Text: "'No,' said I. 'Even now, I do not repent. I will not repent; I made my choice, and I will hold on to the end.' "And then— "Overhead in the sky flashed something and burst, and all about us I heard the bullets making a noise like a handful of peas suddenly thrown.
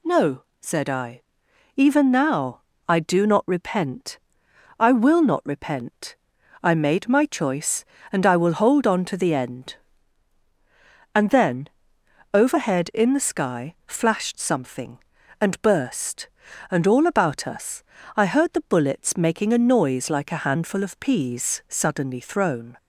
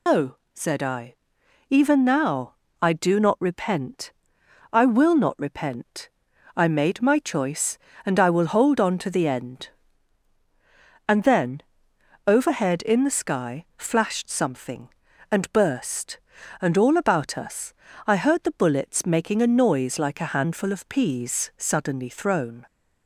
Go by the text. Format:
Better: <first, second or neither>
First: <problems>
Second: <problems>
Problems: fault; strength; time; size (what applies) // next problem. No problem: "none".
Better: first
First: pauses between "us" and "I"; slight; at 17.8 s; 0.34 s long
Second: loses the start of "No"; at 0.0 s; 85 ms // pauses between "us" and "I"; slight; at 17.7 s; 0.34 s long